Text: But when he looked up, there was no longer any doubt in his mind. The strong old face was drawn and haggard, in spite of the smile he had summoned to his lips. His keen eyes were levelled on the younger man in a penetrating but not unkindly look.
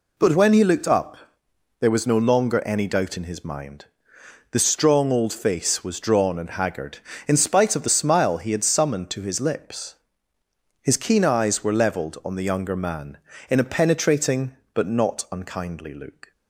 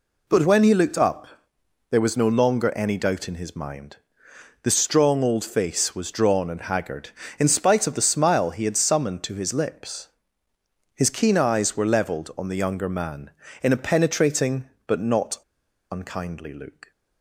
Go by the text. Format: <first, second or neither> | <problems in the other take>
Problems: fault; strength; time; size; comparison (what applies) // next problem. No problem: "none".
first | pauses between "not" and "unkindly"; noticeable; at 15.3 s; 0.52 s long